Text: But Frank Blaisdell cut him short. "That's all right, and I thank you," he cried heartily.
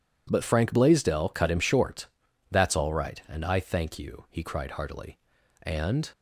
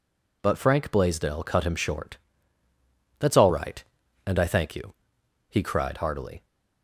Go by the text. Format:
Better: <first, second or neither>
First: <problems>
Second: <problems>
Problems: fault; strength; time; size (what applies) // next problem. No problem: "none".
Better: second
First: goes on to say "And"; slight; from 5.6 s on; 0.48 s long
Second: none